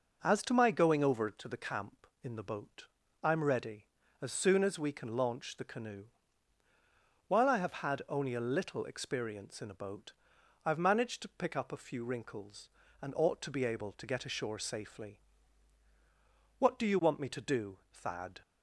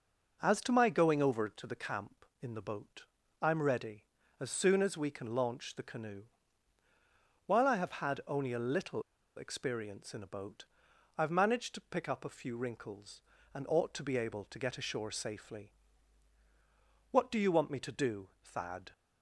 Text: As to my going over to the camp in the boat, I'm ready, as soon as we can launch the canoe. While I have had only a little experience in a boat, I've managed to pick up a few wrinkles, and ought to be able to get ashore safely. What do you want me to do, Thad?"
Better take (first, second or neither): first